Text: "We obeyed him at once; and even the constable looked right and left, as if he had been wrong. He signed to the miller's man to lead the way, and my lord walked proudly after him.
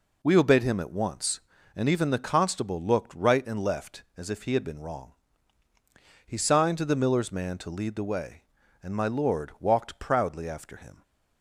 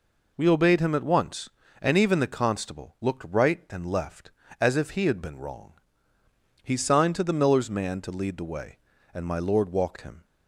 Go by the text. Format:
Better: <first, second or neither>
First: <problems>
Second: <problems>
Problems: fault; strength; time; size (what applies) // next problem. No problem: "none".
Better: first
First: none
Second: skips "proudly after"; at 9.9 s